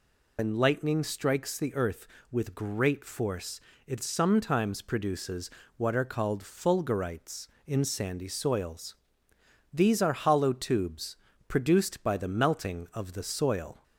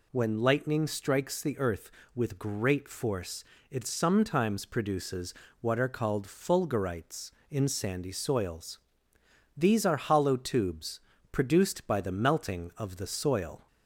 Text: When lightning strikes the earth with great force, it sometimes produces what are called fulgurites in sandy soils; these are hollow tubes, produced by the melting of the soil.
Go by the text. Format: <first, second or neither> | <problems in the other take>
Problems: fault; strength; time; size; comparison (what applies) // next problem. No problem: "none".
second | loses the start of "When"; at 0.3 s; 120 ms // pauses between "produces" and "what"; slight; at 5.5 s; 0.26 s long; slight in the second